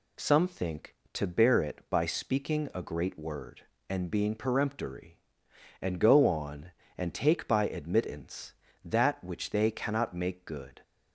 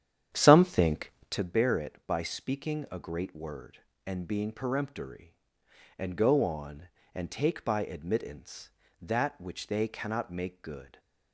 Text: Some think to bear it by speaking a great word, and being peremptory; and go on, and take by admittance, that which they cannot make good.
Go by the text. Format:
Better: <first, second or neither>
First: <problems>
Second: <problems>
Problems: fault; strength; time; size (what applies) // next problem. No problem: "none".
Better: first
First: none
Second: starts louder than the rest; strong; until 1.5 s; 9.5 dB